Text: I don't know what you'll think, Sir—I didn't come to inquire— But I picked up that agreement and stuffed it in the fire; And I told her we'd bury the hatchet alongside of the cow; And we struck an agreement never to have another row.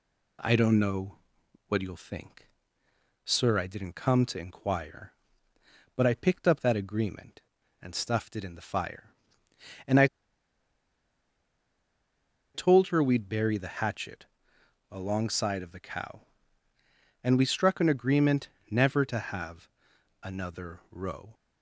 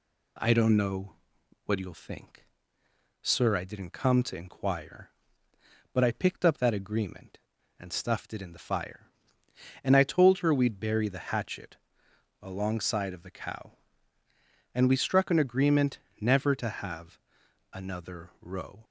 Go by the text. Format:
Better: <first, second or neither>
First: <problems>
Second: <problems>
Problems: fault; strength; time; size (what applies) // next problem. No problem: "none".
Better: second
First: pauses between "know" and "what"; noticeable; at 1.1 s; 0.52 s long // pauses between "I" and "told"; strong; at 10.0 s; 2.4 s long // pauses between "hatchet" and "alongside"; noticeable; at 14.2 s; 0.64 s long // pauses between "agreement" and "never"; slight; at 18.4 s; 0.20 s long // pauses between "have" and "another"; noticeable; at 19.6 s; 0.54 s long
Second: pauses between "know" and "what"; noticeable; at 1.1 s; 0.52 s long // pauses between "hatchet" and "alongside"; noticeable; at 11.7 s; 0.64 s long // pauses between "agreement" and "never"; slight; at 15.9 s; 0.20 s long // pauses between "have" and "another"; noticeable; at 17.1 s; 0.54 s long